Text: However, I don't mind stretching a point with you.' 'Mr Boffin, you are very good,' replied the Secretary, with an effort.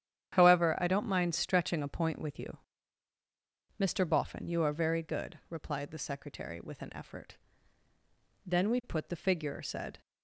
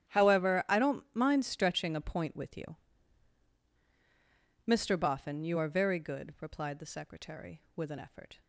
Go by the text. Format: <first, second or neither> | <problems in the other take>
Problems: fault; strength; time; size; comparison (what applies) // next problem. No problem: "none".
second | starts louder than the rest; strong; until 1.3 s; 9.5 dB; strong in the second // goes on to say "Then we put the figure said"; from 8.4 s on; 1.5 s long